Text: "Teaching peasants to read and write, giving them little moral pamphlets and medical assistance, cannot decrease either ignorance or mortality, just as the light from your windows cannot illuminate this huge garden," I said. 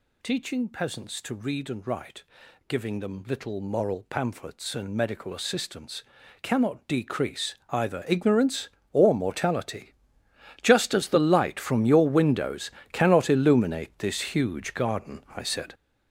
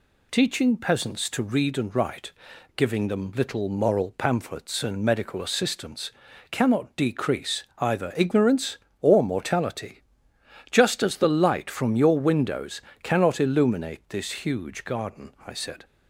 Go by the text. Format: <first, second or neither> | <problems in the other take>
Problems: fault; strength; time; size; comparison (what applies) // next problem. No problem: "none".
second | gets louder; strong; throughout; 9 dB // pauses between "decrease" and "either"; slight; at 7.5 s; 0.16 s long; slight in the second // pauses between "windows" and "cannot"; slight; at 12.6 s; 0.22 s long; slight in the second